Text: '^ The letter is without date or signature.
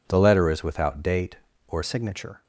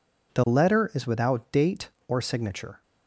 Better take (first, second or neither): second